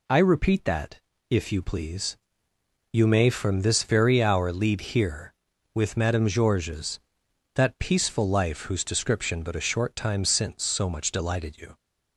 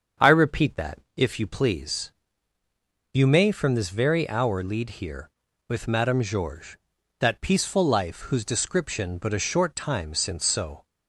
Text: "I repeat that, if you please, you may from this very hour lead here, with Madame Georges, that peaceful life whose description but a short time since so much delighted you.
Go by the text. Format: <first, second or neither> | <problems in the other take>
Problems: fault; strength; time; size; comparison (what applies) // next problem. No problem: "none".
first | starts louder than the rest; until 1.3 s; 7 dB // stops before "much delighted you"; at 10.8 s